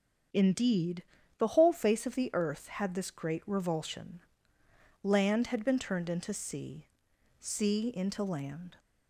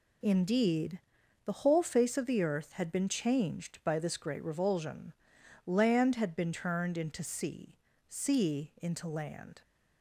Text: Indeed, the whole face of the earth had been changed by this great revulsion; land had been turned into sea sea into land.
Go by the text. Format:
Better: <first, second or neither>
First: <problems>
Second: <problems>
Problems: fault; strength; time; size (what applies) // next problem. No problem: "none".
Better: second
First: starts louder than the rest; strong; until 1.6 s; 7.5 dB // skips "been changed by"; at 2.9 s // pauses between "sea" and "sea"; noticeable; at 6.8 s; 0.56 s long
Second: pauses between "sea" and "sea"; slight; at 7.7 s; 0.36 s long